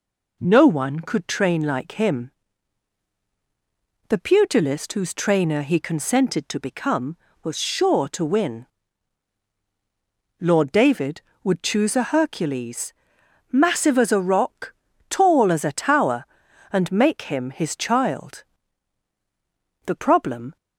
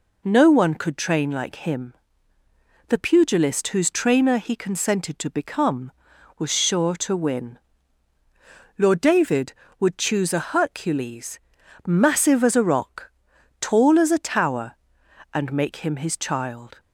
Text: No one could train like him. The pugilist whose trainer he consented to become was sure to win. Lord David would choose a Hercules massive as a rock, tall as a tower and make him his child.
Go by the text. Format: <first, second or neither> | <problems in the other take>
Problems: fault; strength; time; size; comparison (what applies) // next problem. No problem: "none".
second | pauses between "Hercules" and "massive"; noticeable; at 12.9 s; 0.58 s long; noticeable in the second // goes on to say "The problem"; noticeable; from 19.8 s on; 0.70 s long